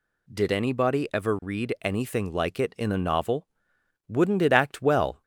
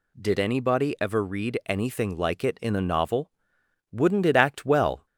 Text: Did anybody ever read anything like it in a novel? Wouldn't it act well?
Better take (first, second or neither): neither